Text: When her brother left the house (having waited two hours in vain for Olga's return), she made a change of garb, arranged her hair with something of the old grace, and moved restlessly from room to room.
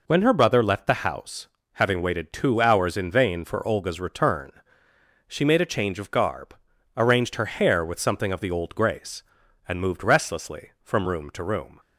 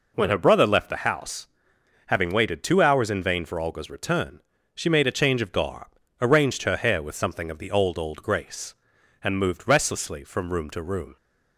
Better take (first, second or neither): first